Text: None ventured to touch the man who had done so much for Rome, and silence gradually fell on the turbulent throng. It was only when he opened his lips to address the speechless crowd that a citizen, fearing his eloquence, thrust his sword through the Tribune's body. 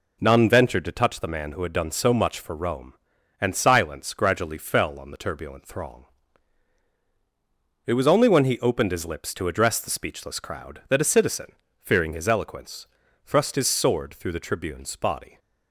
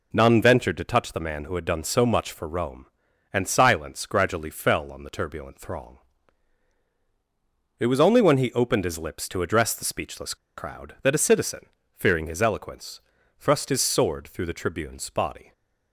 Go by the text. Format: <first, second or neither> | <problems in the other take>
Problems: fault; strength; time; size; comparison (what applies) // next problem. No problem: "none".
first | pauses between "speechless" and "crowd"; slight; at 10.3 s; 0.22 s long